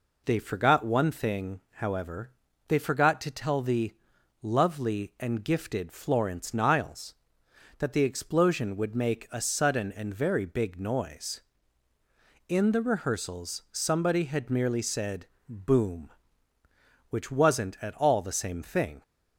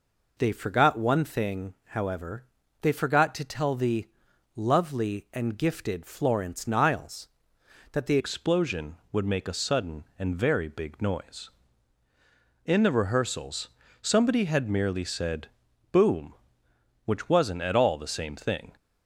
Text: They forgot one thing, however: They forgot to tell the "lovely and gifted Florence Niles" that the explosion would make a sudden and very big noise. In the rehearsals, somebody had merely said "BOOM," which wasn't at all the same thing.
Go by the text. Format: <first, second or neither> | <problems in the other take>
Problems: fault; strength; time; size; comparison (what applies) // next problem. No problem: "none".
first | pauses between "the" and "lovely"; noticeable; at 4.0 s; 0.46 s long; noticeable in the first // changes voice at "explosion"; from 8.1 s on; 10.6 s long // pauses between "said" and "BOOM"; noticeable; at 15.4 s; 0.46 s long; slight in the first